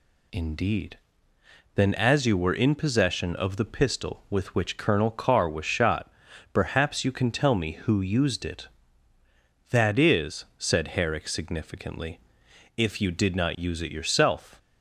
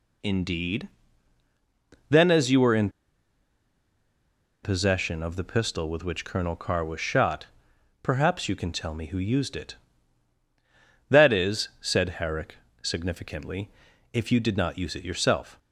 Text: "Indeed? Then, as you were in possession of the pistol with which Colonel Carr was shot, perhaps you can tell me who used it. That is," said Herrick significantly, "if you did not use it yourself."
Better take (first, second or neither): first